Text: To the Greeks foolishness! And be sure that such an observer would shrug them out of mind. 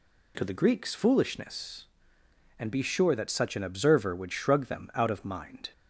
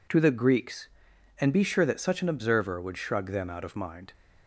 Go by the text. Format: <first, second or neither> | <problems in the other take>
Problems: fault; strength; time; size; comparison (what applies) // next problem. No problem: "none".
first | skips "foolishness"; at 1.1 s